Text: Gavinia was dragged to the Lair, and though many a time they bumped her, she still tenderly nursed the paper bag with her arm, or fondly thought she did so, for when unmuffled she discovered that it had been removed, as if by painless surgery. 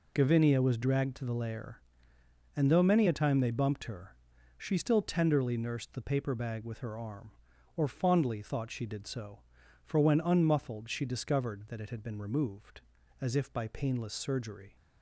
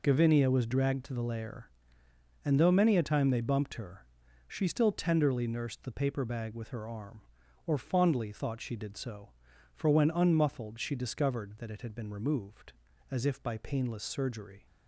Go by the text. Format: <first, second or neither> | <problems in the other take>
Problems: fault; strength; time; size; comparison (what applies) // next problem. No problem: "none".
neither | none